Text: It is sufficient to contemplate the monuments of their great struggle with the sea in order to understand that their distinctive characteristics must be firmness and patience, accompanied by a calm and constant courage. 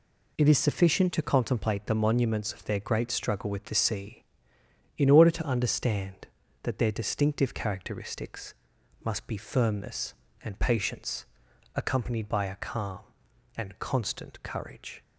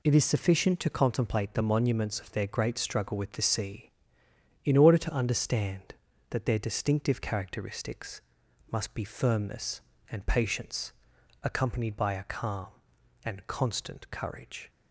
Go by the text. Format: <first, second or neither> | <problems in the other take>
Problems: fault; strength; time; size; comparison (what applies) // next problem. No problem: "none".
neither | pauses between "characteristics" and "must"; noticeable; the same in both